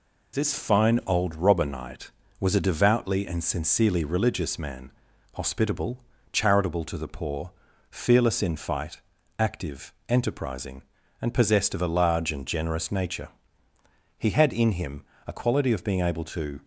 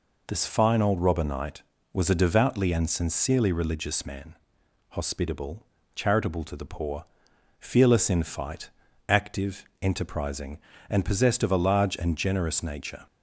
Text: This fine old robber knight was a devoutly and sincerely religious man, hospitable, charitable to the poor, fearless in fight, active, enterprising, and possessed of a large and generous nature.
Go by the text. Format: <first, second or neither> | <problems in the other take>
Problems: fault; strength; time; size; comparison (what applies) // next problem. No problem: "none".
second | goes on to say "He had in him a quality of being able to"; strong; from 14.1 s on; 2.4 s long